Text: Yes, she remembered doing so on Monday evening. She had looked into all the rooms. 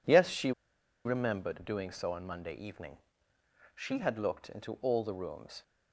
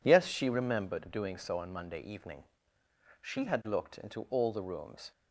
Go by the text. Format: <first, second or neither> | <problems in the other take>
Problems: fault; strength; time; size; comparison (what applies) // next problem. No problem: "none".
second | pauses between "she" and "remembered"; noticeable; at 0.5 s; 0.54 s long